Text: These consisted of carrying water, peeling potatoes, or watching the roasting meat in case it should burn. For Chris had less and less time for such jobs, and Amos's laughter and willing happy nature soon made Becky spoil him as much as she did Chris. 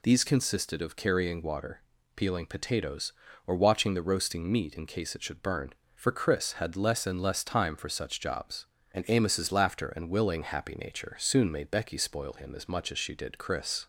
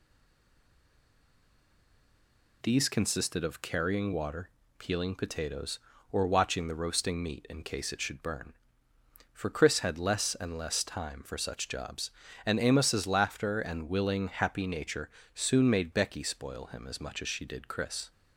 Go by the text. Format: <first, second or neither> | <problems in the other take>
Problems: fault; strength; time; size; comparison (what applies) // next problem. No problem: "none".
first | stays silent before the first word; strong; until 2.6 s; 2.6 s long // pauses between "nature" and "soon"; slight; at 15.0 s; 0.26 s long